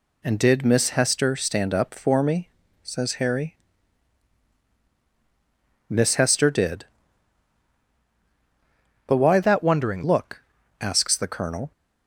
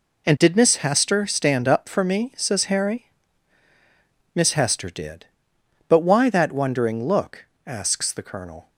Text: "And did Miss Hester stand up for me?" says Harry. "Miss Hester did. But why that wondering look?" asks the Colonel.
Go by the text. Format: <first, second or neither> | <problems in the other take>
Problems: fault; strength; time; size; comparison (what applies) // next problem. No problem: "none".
second | changes voice from "that" to "wondering"; from 9.4 to 10.0 s; 0.6 s long